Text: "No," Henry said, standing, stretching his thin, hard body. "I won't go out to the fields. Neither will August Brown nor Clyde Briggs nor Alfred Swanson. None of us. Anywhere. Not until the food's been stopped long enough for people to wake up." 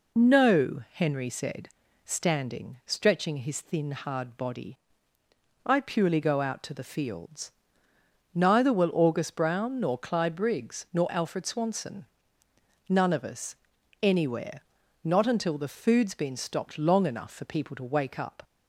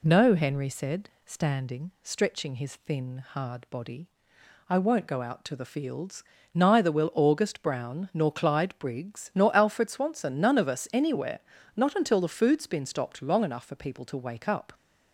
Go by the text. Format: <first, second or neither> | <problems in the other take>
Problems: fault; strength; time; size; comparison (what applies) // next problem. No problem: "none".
second | says "purely" for "won't"; at 5.8 s